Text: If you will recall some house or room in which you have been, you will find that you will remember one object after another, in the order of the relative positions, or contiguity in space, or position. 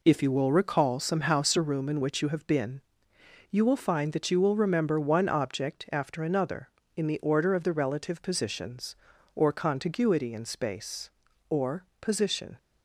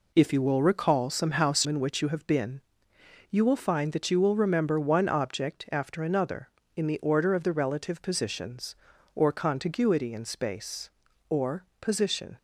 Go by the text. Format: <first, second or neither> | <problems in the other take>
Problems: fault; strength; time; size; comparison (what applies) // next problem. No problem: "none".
first | skips "or room"; at 1.6 s // pauses between "or" and "position"; slight; at 11.6 s; 0.16 s long; slight in the first